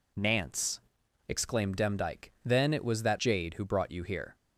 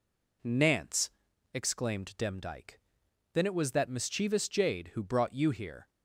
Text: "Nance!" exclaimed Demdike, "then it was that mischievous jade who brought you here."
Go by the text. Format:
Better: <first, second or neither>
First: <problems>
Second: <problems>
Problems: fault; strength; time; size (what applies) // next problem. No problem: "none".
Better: second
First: skips "mischievous"; at 3.1 s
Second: none